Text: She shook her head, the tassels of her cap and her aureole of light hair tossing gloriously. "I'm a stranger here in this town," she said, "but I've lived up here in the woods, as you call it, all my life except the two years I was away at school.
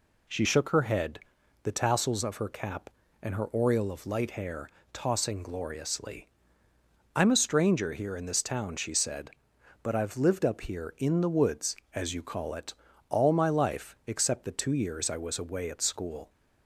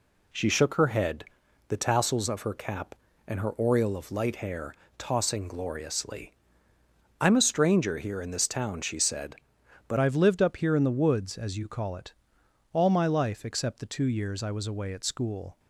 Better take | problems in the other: first | pauses between "hair" and "tossing"; slight; at 4.7 s; 0.22 s long; slight in the first // changes voice at "I've"; from 9.9 s on; 5.6 s long

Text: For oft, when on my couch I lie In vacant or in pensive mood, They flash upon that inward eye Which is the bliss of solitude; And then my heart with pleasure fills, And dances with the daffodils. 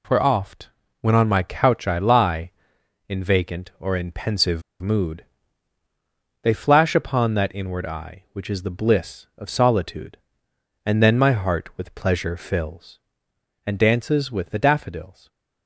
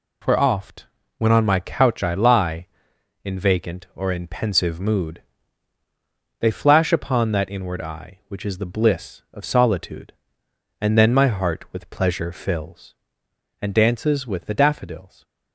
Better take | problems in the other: second | pauses between "pensive" and "mood"; slight; at 4.6 s; 0.20 s long // stays silent after the last word; slight; from 15.1 s on; 0.5 s long

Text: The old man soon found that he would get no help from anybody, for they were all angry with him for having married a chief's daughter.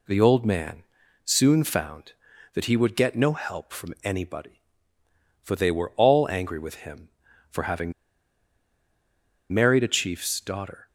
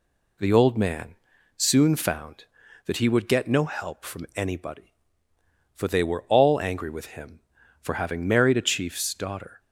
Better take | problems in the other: second | pauses between "man" and "soon"; at 0.8 s; 0.40 s long; also in the second // pauses between "having" and "married"; strong; at 7.9 s; 1.6 s long

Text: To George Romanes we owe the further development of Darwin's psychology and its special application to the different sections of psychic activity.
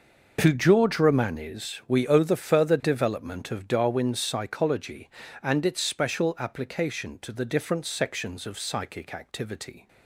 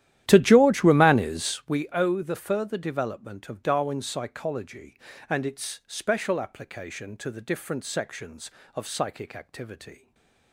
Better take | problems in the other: first | starts louder than the rest; strong; until 1.7 s; 12.5 dB // stays silent after the last word; slight; from 9.9 s on; 0.6 s long

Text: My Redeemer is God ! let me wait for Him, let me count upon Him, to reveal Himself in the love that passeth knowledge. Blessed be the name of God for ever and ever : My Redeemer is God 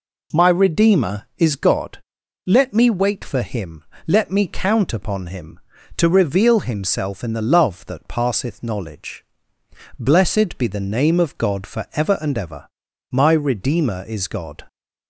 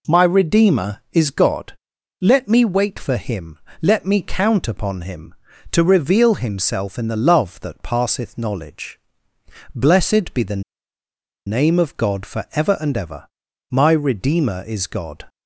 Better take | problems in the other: first | pauses between "the" and "name"; noticeable; at 10.6 s; 0.84 s long

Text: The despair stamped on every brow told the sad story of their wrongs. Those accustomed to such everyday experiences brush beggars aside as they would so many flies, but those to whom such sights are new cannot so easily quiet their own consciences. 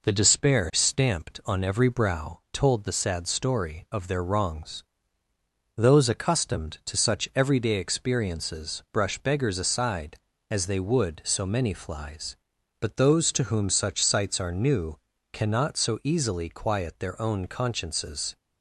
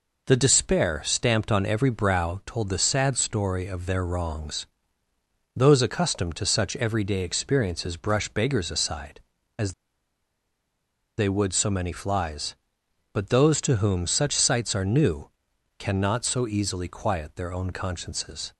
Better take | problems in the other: first | pauses between "as" and "they"; strong; at 9.7 s; 1.4 s long // pauses between "new" and "cannot"; noticeable; at 15.2 s; 0.48 s long; slight in the first

